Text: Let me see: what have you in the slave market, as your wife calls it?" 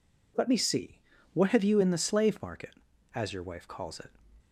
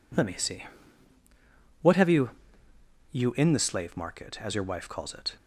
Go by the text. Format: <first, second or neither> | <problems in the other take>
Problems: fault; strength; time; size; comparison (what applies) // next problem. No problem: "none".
first | says "you" twice; at 3.1 s